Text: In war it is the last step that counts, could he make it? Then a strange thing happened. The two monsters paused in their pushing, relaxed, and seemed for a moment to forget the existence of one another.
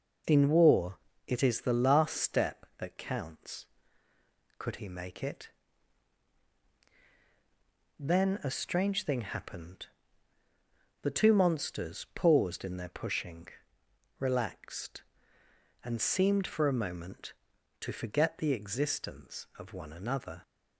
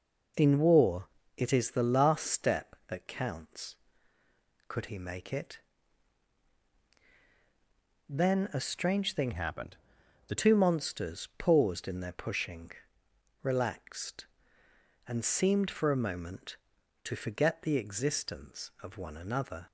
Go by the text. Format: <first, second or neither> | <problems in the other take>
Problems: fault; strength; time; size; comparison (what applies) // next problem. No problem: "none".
first | pauses between "war" and "it"; slight; at 1.0 s; 0.28 s long; slight in the first // changes voice from "happened" to "The"; from 9.3 to 10.3 s; 1.0 s long